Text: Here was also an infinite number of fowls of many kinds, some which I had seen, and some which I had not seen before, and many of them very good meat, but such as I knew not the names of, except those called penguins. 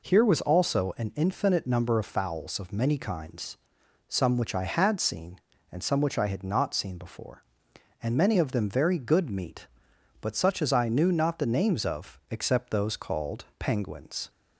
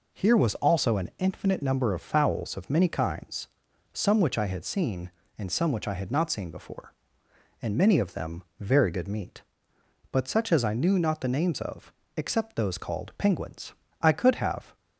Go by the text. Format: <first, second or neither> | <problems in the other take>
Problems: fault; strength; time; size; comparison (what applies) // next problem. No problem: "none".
first | pauses between "them" and "very"; slight; at 8.4 s; 0.16 s long // goes on to say "I could have"; noticeable; from 14.0 s on; 0.76 s long